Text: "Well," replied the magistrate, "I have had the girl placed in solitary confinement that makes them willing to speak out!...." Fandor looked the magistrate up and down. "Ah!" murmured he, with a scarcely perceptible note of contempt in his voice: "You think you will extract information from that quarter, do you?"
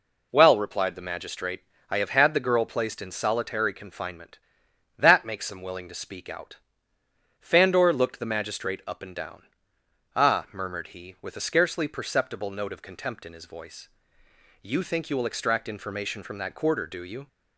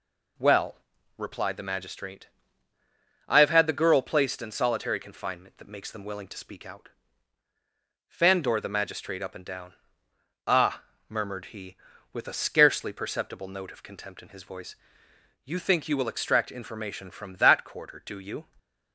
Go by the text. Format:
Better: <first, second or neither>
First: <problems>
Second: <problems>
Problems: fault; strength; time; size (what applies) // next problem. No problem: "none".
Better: first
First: none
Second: skips "looked"; at 8.5 s